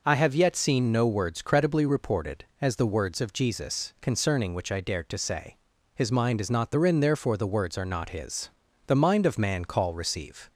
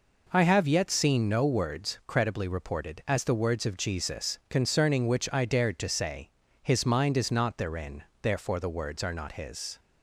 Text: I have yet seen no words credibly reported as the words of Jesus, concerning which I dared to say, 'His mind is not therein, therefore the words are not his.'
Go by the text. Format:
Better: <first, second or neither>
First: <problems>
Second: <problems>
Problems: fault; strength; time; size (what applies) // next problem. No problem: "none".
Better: second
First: goes on to say "The mind of man call receive"; from 8.8 s on; 1.6 s long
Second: none